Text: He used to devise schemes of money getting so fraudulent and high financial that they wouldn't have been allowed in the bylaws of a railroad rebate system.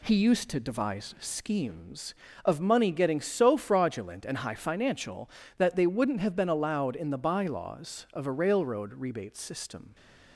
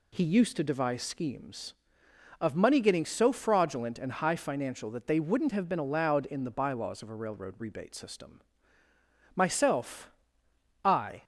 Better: first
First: none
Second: goes on to say "Myself I"; strong; from 9.3 s on; 1.8 s long

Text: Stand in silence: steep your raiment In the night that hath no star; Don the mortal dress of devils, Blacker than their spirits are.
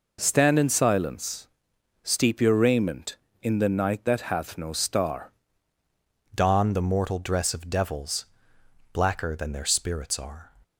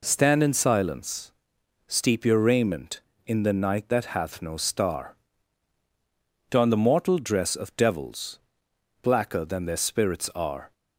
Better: second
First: changes voice at "Don"; from 6.3 s on; 4.2 s long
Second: none

